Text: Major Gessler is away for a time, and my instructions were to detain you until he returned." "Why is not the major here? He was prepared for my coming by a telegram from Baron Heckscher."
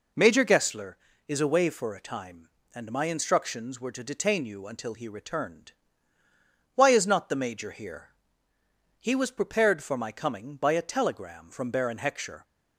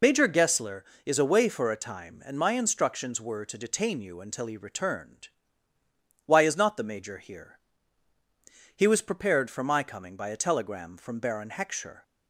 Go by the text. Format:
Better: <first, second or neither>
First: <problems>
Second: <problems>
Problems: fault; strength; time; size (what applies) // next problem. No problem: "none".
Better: first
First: none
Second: loses the start of "Major"; at 0.0 s; 55 ms